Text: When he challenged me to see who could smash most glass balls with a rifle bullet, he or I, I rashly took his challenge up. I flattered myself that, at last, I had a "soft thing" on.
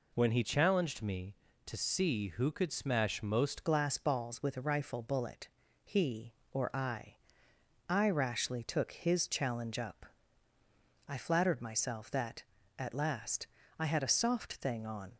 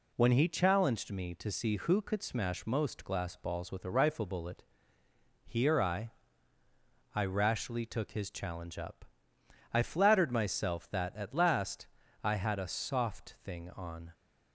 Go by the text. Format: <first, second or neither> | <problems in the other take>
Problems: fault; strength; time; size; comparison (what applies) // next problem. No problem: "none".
second | changes voice at "glass"; from 3.6 s on; 11.5 s long